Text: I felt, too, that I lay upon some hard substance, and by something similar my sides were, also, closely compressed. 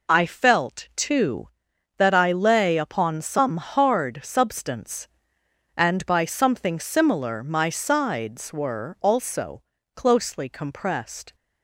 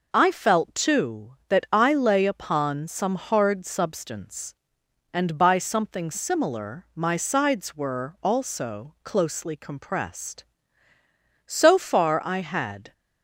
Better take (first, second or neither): first